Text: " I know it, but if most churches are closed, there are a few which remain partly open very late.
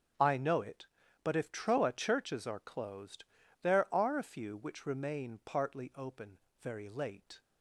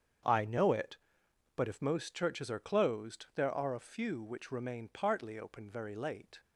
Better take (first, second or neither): second